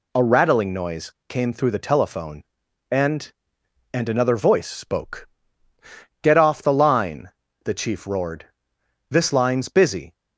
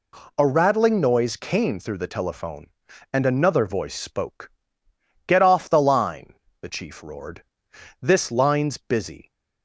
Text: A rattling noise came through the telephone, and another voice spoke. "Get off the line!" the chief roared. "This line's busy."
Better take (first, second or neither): second